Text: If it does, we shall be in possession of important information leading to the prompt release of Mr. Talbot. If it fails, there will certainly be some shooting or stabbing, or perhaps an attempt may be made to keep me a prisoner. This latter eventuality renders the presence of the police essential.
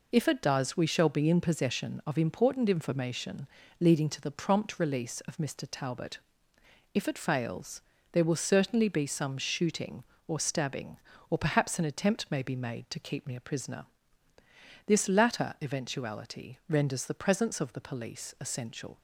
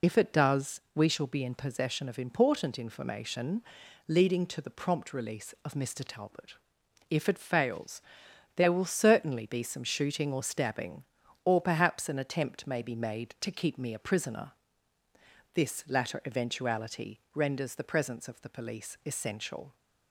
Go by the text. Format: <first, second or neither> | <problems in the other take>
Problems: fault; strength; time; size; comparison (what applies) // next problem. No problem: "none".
first | loses the start of "If"; at 0.0 s; 50 ms // pauses between "information" and "leading"; at 3.6 s; 0.44 s long; slight in the first